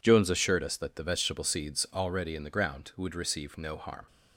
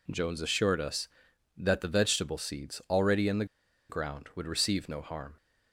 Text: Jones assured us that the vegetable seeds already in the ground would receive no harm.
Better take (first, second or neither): first